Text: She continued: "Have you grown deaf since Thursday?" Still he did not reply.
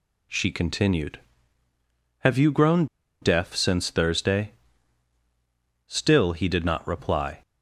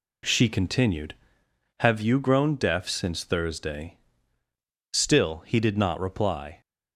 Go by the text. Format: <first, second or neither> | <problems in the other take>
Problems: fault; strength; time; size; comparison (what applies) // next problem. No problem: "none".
second | pauses between "grown" and "deaf"; slight; at 2.8 s; 0.35 s long